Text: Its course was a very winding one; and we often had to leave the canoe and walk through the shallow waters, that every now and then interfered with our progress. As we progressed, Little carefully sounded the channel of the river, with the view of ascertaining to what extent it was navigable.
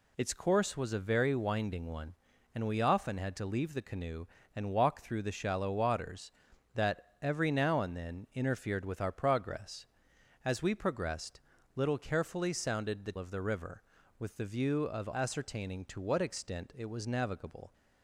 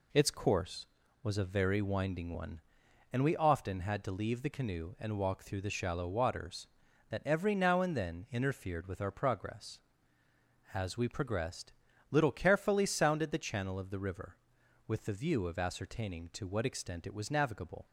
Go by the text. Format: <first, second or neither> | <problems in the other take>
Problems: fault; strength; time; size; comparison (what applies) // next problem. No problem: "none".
second | skips "channel"; at 13.1 s